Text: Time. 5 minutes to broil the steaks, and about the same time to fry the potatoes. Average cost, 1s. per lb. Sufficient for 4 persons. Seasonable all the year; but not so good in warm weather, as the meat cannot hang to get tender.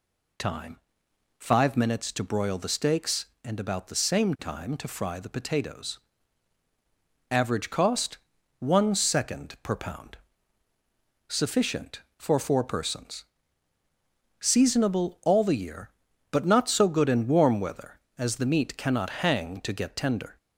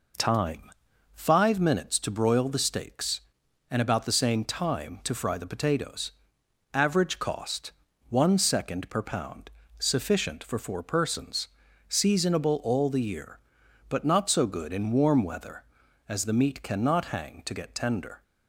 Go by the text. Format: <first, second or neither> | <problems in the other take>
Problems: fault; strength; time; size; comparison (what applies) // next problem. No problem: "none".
neither | none